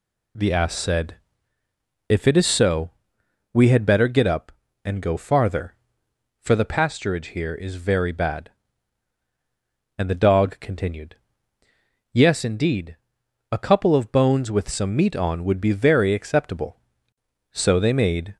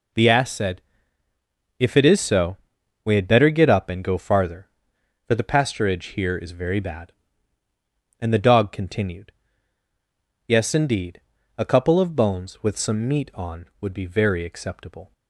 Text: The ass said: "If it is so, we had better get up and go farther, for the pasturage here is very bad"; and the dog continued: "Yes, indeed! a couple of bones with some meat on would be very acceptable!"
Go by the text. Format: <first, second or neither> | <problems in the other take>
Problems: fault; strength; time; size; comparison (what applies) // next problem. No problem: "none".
second | goes on to say "So they made"; noticeable; from 17.5 s on; 0.86 s long